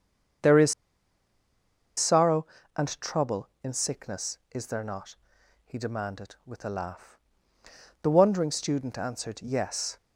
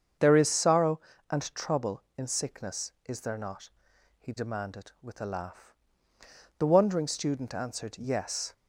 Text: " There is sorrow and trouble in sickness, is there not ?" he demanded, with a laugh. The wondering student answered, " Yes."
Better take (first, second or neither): second